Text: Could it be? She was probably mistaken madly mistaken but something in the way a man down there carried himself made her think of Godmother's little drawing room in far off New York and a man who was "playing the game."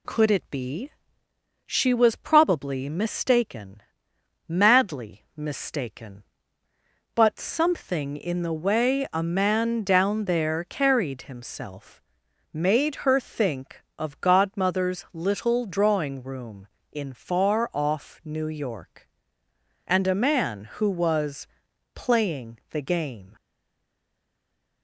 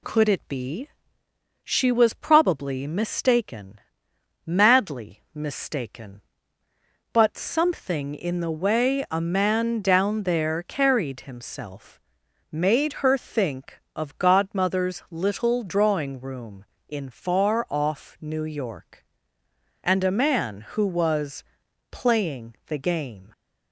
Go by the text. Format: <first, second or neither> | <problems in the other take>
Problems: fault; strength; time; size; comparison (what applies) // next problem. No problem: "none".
second | pauses between "mistaken" and "madly"; noticeable; at 3.8 s; 0.66 s long; noticeable in the second // pauses between "himself" and "made"; noticeable; at 11.9 s; 0.54 s long; noticeable in the second // pauses between "was" and "playing"; noticeable; at 21.4 s; 0.48 s long; noticeable in the second // stays silent after the last word; noticeable; from 23.3 s on; 1.5 s long